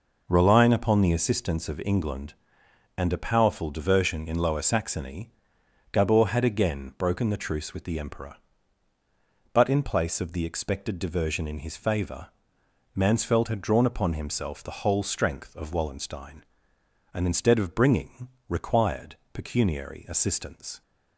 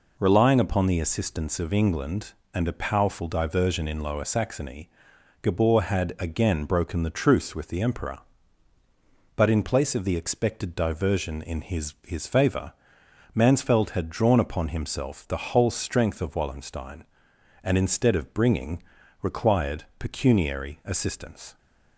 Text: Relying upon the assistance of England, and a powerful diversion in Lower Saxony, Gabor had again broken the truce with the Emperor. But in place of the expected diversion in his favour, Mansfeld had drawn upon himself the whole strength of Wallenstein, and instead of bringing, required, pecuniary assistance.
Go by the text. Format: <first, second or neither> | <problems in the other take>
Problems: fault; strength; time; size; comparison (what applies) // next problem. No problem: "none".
first | says "his" twice; at 12.0 s